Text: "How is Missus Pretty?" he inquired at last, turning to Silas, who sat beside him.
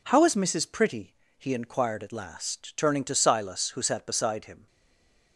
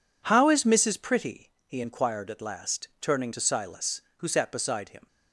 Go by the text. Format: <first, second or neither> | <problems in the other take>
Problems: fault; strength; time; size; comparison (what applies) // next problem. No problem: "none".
second | stays silent after the last word; slight; from 4.6 s on; 0.7 s long